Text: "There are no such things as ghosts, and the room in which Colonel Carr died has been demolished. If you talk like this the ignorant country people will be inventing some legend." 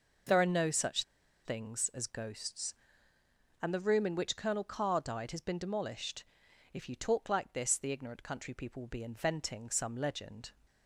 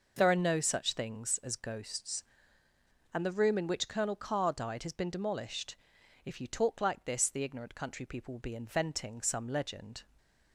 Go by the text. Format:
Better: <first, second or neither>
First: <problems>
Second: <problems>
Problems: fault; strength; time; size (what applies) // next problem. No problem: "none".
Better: second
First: pauses between "such" and "things"; at 1.0 s; 0.41 s long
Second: none